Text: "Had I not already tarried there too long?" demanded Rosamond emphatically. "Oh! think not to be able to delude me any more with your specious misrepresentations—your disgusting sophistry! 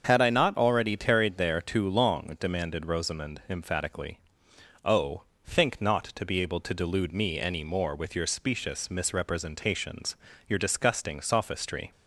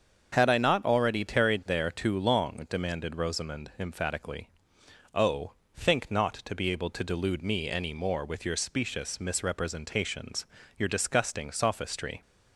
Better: neither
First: starts louder than the rest; until 1.0 s; 7 dB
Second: starts louder than the rest; until 1.3 s; 7 dB

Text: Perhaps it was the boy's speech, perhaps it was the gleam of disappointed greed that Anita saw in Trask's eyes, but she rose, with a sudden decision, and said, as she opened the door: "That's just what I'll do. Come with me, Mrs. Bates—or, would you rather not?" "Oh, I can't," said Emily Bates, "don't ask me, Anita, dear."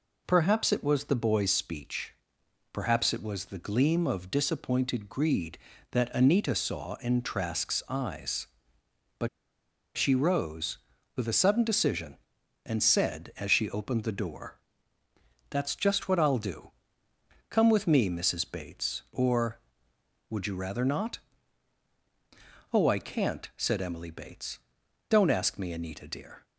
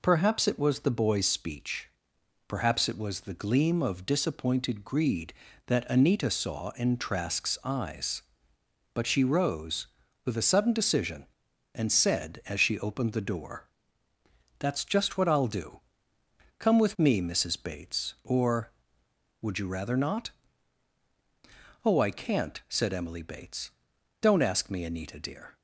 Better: second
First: pauses between "but" and "she"; noticeable; at 9.2 s; 0.67 s long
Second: none

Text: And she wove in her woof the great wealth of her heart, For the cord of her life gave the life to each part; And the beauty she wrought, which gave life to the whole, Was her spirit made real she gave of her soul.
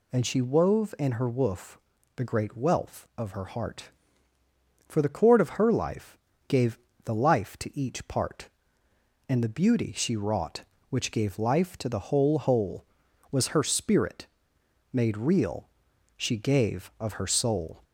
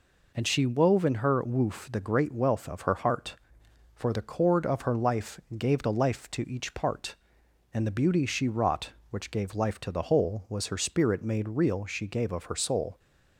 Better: second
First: pauses between "woof" and "the"; at 1.7 s; 0.38 s long // pauses between "life" and "gave"; slight; at 6.1 s; 0.30 s long // pauses between "gave" and "the"; slight; at 6.7 s; 0.28 s long // says "whole" twice; at 12.3 s // pauses between "spirit" and "made"; noticeable; at 14.2 s; 0.64 s long // pauses between "real" and "she"; noticeable; at 15.6 s; 0.48 s long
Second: pauses between "life" and "gave"; slight; at 5.4 s; 0.16 s long

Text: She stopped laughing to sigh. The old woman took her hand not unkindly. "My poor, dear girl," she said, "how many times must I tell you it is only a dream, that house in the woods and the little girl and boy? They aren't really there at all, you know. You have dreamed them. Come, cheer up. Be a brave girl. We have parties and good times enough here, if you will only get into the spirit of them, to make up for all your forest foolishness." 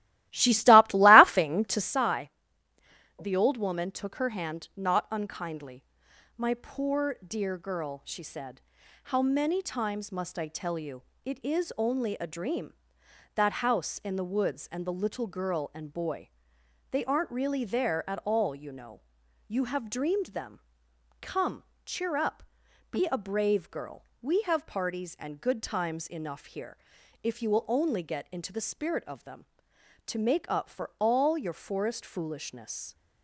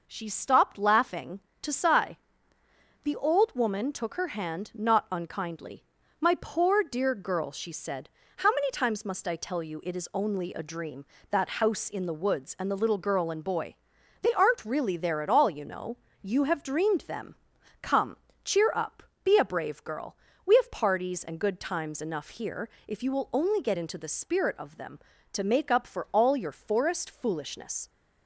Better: second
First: starts louder than the rest; strong; until 2.0 s; 16.5 dB // pauses between "you" and "it"; slight; at 11.0 s; 0.24 s long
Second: none

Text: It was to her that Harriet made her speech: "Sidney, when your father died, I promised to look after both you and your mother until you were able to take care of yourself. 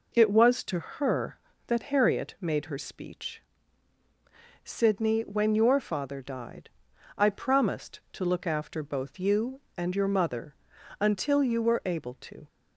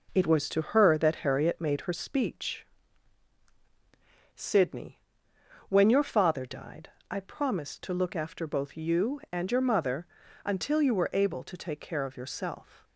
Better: second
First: pauses between "mother" and "until"; noticeable; at 10.5 s; 0.48 s long // stops before "take care of yourself"; at 12.4 s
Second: pauses between "mother" and "until"; slight; at 10.0 s; 0.36 s long

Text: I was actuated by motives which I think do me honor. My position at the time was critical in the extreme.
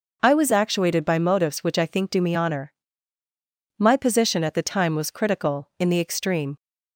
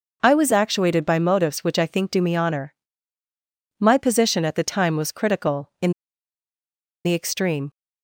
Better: first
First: none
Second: pauses between "in" and "the"; at 5.9 s; 1.1 s long

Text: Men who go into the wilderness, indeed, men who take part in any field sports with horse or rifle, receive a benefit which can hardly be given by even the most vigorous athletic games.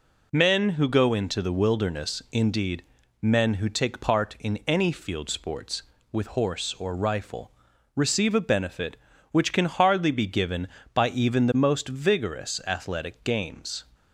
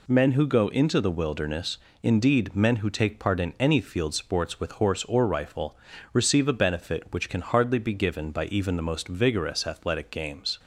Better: neither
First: none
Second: none

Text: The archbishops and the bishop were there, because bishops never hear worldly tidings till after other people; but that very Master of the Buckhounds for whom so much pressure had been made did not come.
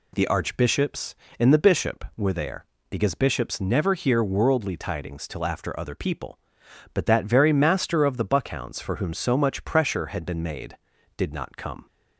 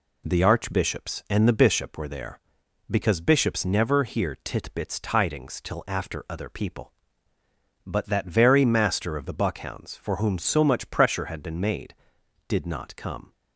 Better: first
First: none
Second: says "titbits" for "worldly"; at 4.4 s

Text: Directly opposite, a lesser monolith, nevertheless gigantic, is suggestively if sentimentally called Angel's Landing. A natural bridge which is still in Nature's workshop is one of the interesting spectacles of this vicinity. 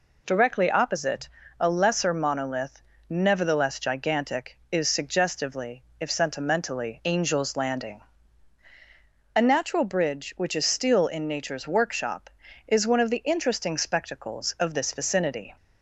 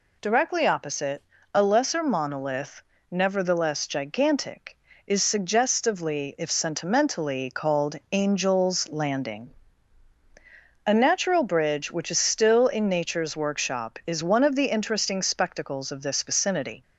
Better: second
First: pauses between "suggestively" and "if"; slight; at 5.8 s; 0.16 s long // skips "called"; at 7.0 s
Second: none

